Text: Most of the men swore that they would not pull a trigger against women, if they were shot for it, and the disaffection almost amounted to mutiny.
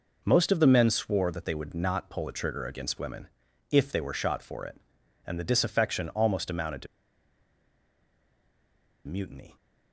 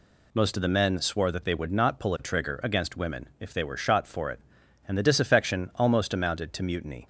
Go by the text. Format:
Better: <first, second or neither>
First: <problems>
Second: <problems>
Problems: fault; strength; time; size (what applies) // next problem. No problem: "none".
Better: second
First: pauses between "to" and "mutiny"; strong; at 6.8 s; 2.2 s long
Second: none